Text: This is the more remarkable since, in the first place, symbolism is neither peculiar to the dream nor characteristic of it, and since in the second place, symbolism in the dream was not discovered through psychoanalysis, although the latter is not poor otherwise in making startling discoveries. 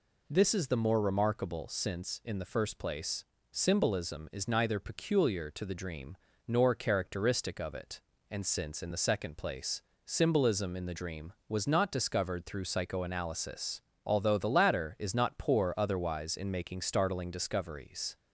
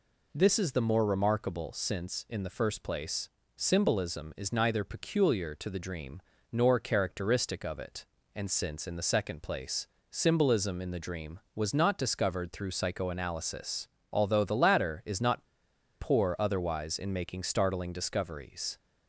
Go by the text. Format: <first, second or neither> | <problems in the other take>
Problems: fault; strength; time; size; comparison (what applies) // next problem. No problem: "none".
first | pauses between "dream" and "nor"; slight; at 6.2 s; 0.30 s long; slight in the first // pauses between "not" and "poor"; noticeable; at 15.4 s; 0.58 s long